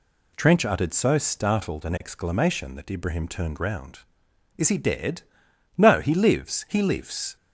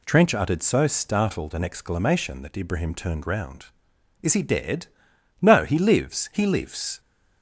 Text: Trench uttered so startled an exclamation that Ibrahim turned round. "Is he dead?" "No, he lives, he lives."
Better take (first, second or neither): neither